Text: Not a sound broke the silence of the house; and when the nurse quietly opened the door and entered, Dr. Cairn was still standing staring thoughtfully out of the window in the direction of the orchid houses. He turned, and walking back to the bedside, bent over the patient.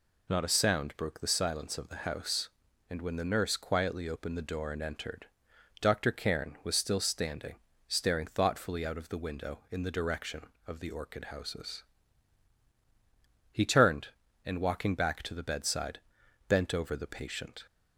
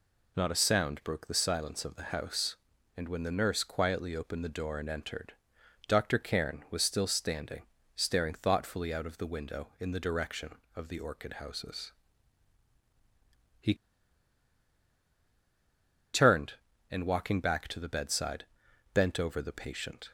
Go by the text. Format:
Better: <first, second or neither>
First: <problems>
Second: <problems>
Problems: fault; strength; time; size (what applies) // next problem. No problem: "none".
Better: first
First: pauses between "standing" and "staring"; slight; at 7.5 s; 0.33 s long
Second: pauses between "standing" and "staring"; slight; at 7.6 s; 0.34 s long // pauses between "He" and "turned"; strong; at 13.7 s; 2.3 s long